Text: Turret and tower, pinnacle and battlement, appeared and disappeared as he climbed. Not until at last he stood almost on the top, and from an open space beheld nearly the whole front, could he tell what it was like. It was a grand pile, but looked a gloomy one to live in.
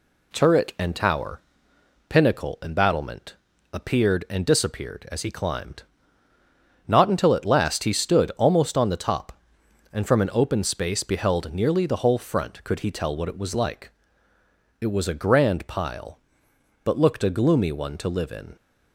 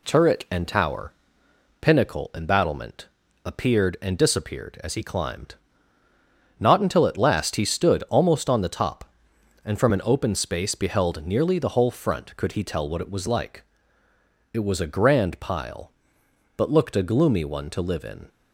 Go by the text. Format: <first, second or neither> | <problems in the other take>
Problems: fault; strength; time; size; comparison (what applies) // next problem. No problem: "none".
neither | none